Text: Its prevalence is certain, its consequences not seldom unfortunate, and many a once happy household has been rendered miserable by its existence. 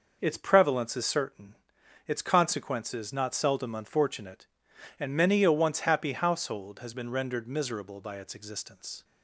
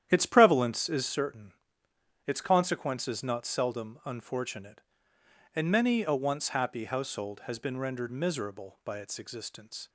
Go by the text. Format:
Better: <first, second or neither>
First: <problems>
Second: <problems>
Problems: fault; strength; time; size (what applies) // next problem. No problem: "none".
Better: first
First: none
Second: starts louder than the rest; strong; until 1.3 s; 10.5 dB